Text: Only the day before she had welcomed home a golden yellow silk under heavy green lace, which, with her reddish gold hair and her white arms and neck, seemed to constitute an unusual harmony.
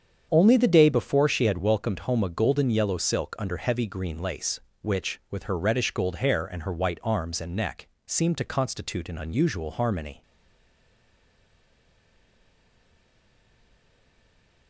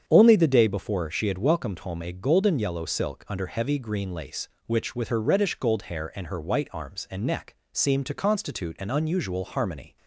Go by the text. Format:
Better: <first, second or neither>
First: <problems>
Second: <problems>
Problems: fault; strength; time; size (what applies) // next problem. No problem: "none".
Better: second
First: starts louder than the rest; strong; until 1.3 s; 7.5 dB // stays silent after the last word; strong; from 10.2 s on; 4.4 s long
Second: starts louder than the rest; strong; until 1.0 s; 8 dB